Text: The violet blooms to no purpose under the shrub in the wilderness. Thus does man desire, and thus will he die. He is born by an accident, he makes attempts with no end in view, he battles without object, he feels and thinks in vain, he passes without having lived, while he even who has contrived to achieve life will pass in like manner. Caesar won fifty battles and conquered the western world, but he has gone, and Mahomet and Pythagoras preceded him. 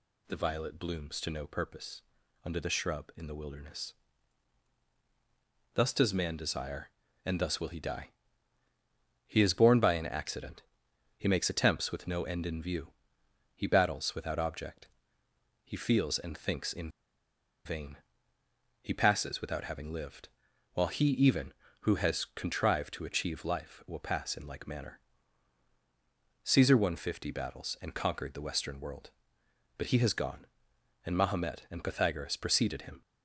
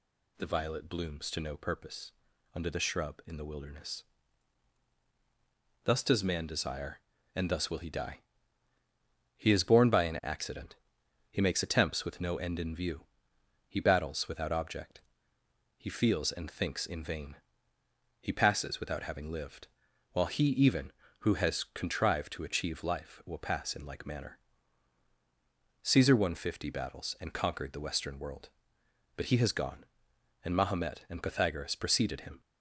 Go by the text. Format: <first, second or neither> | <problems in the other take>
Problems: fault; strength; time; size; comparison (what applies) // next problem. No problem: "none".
second | pauses between "purpose" and "under"; at 2.0 s; 0.42 s long; also in the second // pauses between "in" and "vain"; noticeable; at 16.8 s; 0.76 s long